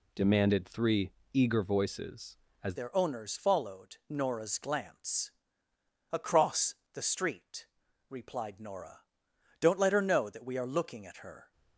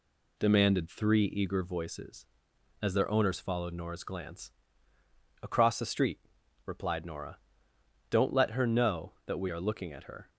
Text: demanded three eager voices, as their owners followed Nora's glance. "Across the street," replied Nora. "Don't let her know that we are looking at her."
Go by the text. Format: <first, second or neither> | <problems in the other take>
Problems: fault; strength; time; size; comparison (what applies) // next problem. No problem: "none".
second | pauses between "three" and "eager"; slight; at 1.1 s; 0.22 s long // changes voice at "their"; from 2.7 s on; 8.8 s long // pauses between "Across" and "the"; slight; at 6.7 s; 0.18 s long